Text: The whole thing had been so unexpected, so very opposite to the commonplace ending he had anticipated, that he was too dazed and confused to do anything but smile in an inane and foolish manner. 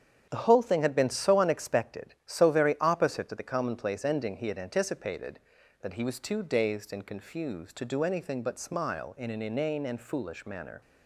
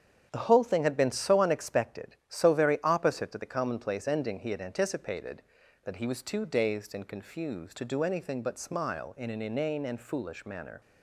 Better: neither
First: starts louder than the rest; strong; until 1.3 s; 8.5 dB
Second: starts louder than the rest; strong; until 1.3 s; 8.5 dB

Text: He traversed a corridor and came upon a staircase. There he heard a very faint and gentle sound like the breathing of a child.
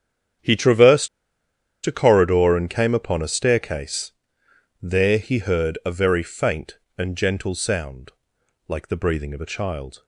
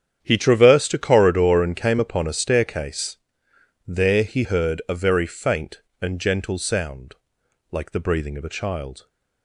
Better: second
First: starts louder than the rest; strong; until 2.1 s; 9 dB // pauses between "traversed" and "a"; noticeable; at 1.0 s; 0.77 s long // pauses between "sound" and "like"; noticeable; at 8.1 s; 0.56 s long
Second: starts louder than the rest; strong; until 1.2 s; 9 dB // pauses between "sound" and "like"; noticeable; at 7.1 s; 0.56 s long

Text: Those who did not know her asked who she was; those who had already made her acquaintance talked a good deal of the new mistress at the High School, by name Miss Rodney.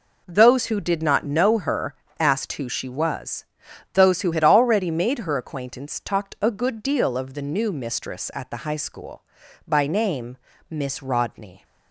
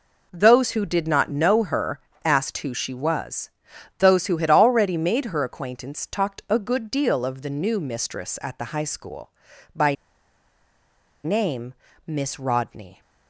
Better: first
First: pauses between "her" and "asked"; slight; at 1.9 s; 0.26 s long // pauses between "name" and "Miss"; slight; at 10.3 s; 0.34 s long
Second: pauses between "her" and "asked"; slight; at 1.9 s; 0.26 s long // pauses between "by" and "name"; strong; at 9.9 s; 1.2 s long // pauses between "name" and "Miss"; slight; at 11.7 s; 0.34 s long

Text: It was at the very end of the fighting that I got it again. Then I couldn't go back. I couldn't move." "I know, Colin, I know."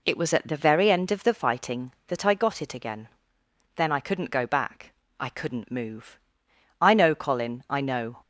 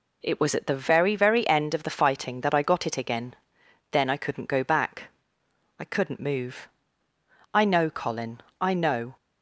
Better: first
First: none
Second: says "very" twice; at 1.1 s

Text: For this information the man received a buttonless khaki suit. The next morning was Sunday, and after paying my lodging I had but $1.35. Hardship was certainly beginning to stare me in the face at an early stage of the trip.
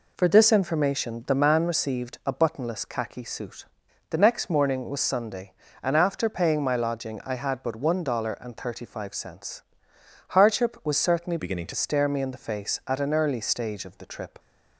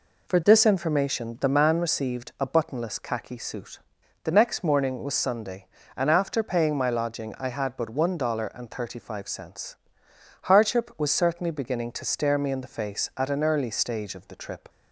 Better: second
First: changes voice from "beginning" to "to"; from 11.3 to 11.7 s; 0.4 s long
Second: none

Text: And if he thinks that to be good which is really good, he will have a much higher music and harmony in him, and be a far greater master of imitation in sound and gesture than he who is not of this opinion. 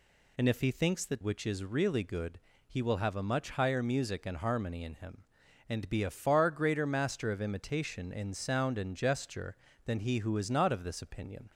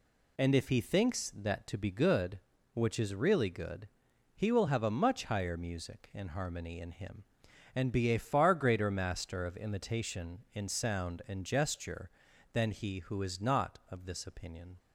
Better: second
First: skips "to be good"; at 1.2 s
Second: none

